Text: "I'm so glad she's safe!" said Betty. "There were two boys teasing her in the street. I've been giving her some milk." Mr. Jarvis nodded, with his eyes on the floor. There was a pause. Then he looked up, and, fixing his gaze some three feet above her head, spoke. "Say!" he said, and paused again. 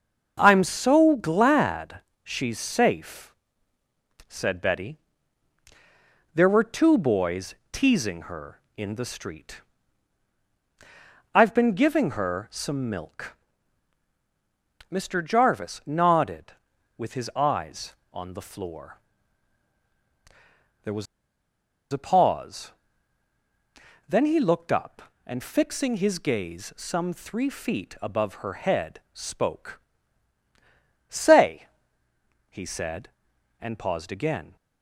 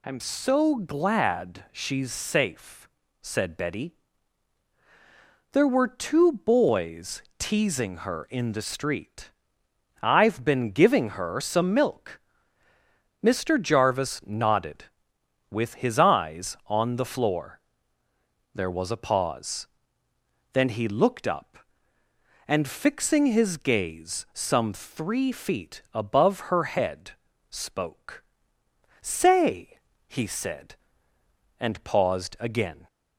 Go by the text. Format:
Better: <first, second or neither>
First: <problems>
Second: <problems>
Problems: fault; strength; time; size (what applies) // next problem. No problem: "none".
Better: second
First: starts louder than the rest; until 1.3 s; 6.5 dB // pauses between "glad" and "she's"; slight; at 2.0 s; 0.22 s long // pauses between "boys" and "teasing"; slight; at 7.5 s; 0.18 s long // pauses between "was" and "a"; noticeable; at 21.0 s; 0.87 s long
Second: pauses between "boys" and "teasing"; slight; at 7.2 s; 0.16 s long